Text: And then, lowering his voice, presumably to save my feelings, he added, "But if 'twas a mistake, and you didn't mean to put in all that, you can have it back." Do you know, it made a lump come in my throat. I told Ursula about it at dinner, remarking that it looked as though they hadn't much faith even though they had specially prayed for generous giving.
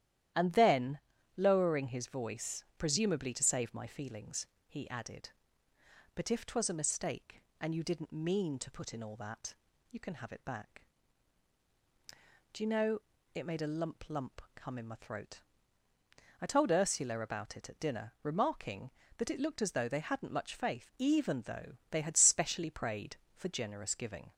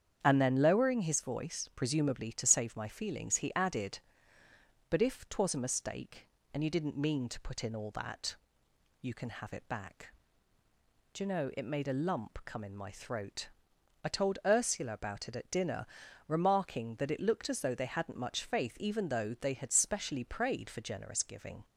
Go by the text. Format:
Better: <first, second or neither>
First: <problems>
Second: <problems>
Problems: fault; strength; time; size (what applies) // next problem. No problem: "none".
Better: second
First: starts louder than the rest; strong; until 1.7 s; 12 dB // says "lump" twice; at 14.0 s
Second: starts louder than the rest; strong; until 1.2 s; 8.5 dB